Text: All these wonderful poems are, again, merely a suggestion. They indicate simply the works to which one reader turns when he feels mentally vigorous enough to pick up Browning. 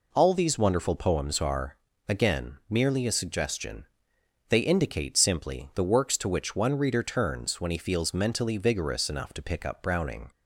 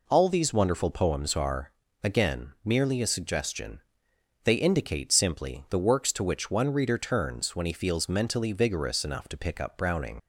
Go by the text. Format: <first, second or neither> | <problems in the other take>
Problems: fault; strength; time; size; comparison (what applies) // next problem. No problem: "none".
first | leaves "Browning" unfinished; at 10.1 s; 55 ms